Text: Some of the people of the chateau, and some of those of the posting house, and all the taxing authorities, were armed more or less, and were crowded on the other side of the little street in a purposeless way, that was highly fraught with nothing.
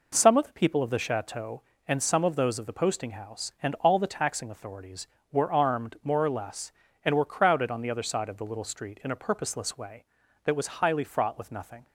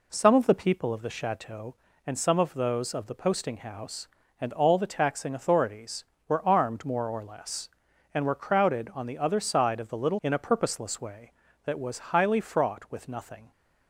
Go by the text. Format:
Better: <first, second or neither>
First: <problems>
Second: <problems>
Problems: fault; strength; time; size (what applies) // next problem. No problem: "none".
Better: first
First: none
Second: skips "street"; at 10.1 s